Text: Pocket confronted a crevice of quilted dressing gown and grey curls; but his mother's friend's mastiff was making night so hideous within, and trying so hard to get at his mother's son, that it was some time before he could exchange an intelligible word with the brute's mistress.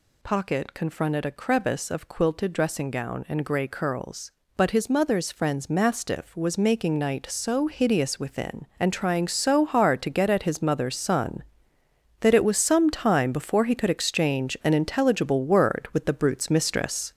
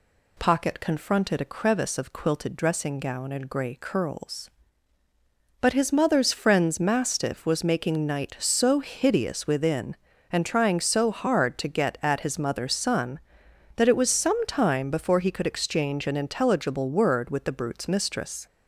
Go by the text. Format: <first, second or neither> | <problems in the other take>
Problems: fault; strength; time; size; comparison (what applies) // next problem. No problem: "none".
second | gets louder; throughout; 6 dB